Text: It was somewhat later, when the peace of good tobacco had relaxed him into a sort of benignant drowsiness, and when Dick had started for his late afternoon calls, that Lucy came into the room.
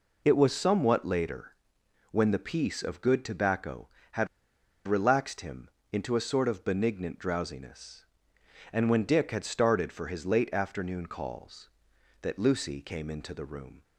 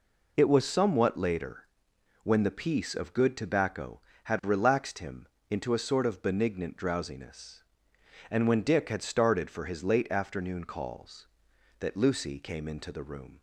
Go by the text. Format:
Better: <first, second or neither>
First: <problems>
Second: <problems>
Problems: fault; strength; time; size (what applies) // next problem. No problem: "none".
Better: second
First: pauses between "had" and "relaxed"; noticeable; at 4.2 s; 0.59 s long // pauses between "him" and "into"; slight; at 5.6 s; 0.22 s long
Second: pauses between "him" and "into"; slight; at 5.2 s; 0.22 s long